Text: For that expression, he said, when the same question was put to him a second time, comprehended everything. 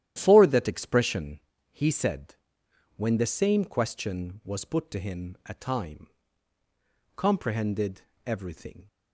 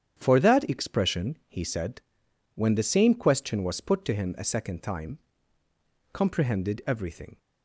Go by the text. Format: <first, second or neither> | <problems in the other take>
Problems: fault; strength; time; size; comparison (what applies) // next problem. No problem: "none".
second | starts louder than the rest; strong; until 1.1 s; 11.5 dB; strong in the second // skips "second"; at 5.5 s // pauses between "comprehended" and "everything"; slight; at 8.0 s; 0.24 s long